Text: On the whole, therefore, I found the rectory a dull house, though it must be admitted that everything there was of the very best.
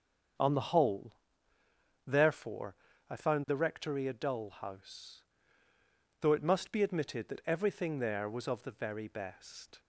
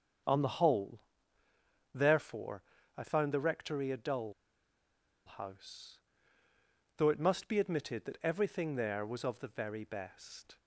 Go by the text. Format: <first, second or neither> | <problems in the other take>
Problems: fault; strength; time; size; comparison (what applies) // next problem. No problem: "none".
first | starts louder than the rest; strong; until 2.2 s; 7 dB; strong in the first // pauses between "dull" and "house"; noticeable; at 4.3 s; 0.93 s long